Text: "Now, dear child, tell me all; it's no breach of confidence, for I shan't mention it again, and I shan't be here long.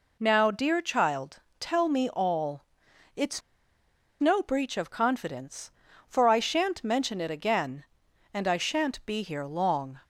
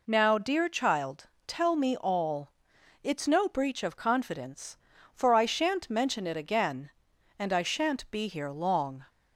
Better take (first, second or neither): second